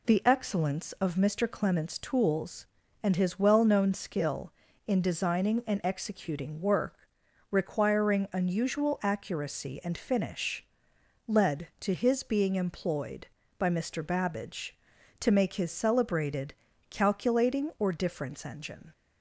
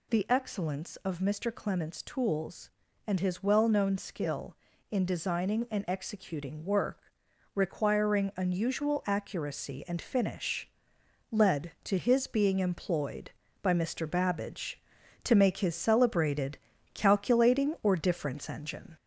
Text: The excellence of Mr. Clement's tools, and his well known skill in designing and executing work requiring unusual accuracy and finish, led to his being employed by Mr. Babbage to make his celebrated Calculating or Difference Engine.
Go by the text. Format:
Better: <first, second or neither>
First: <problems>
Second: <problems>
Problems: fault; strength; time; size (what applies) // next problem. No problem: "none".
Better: first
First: pauses between "work" and "requiring"; noticeable; at 6.9 s; 0.56 s long // pauses between "celebrated" and "Calculating"; slight; at 16.5 s; 0.36 s long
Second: gets louder; throughout; 3.5 dB // pauses between "work" and "requiring"; noticeable; at 6.9 s; 0.56 s long // pauses between "celebrated" and "Calculating"; slight; at 16.5 s; 0.36 s long